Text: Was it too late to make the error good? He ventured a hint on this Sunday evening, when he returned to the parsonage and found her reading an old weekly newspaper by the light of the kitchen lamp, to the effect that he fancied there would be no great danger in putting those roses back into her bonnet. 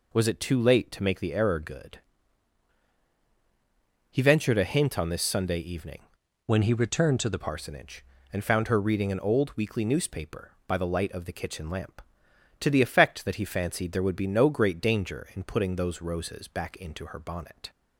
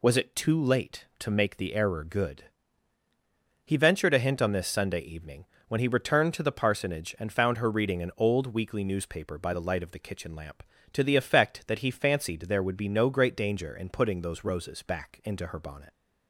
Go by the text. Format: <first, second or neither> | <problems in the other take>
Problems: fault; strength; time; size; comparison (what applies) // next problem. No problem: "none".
second | changes voice from "when" to "the"; from 6.4 to 7.4 s; 1.0 s long